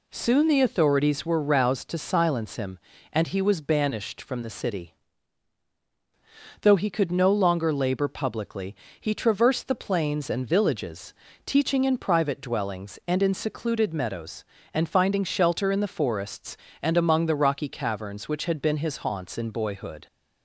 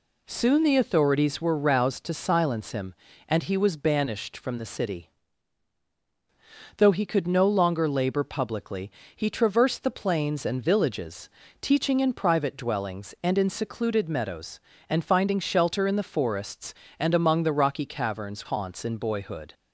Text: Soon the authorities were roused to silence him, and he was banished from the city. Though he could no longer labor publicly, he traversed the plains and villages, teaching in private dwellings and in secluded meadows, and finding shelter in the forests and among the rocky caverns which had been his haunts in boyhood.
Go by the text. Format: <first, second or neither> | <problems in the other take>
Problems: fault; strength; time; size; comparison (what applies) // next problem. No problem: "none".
first | skips "which had been his"; at 18.4 s